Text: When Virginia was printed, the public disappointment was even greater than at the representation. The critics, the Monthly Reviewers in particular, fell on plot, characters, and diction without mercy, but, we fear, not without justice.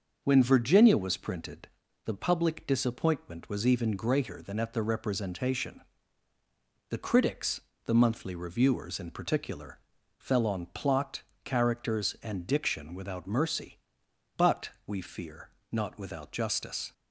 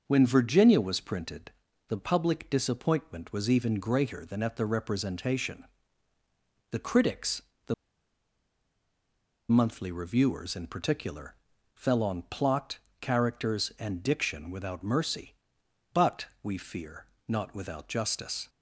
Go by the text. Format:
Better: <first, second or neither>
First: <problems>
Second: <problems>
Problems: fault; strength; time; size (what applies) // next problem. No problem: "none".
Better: first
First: starts louder than the rest; until 1.2 s; 6.5 dB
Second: starts louder than the rest; until 1.0 s; 6 dB // pauses between "the" and "Monthly"; strong; at 7.7 s; 1.7 s long